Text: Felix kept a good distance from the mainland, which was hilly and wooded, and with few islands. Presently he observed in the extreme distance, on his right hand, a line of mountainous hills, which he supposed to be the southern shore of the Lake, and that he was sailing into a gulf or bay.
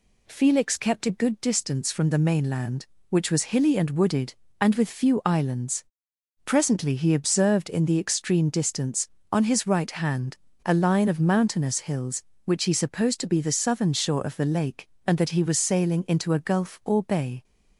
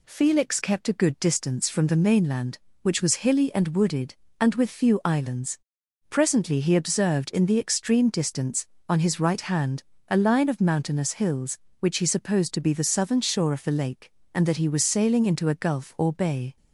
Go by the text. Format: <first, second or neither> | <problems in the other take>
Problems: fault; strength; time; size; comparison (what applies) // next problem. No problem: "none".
neither | none